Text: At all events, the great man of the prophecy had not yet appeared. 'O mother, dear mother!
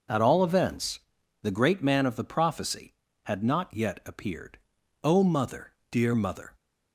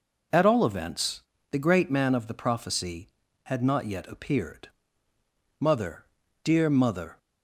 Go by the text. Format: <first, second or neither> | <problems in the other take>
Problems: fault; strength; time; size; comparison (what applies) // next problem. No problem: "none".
first | skips "O"; at 5.1 s